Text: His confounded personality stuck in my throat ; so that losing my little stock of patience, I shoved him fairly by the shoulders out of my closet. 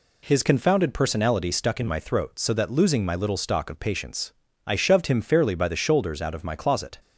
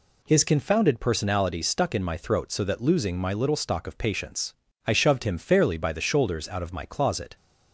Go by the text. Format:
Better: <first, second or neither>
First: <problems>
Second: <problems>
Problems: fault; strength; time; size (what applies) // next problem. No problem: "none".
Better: neither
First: none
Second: none